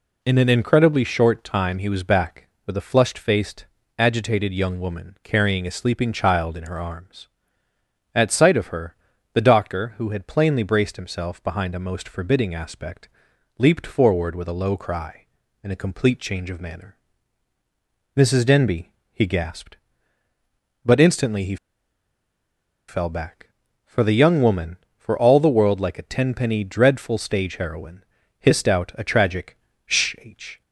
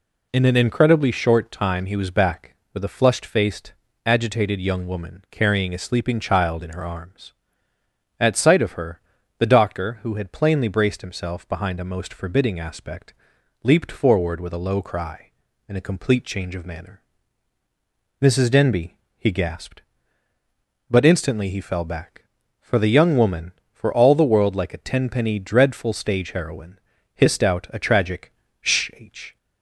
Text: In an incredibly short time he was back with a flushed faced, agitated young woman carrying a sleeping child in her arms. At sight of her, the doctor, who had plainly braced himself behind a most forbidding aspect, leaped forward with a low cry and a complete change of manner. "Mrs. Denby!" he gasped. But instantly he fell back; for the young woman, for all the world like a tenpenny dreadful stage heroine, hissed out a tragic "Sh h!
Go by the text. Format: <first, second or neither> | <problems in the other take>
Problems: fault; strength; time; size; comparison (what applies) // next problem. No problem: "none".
second | pauses between "he" and "fell"; strong; at 21.5 s; 1.3 s long // pauses between "tragic" and "Sh"; slight; at 29.5 s; 0.28 s long; slight in the second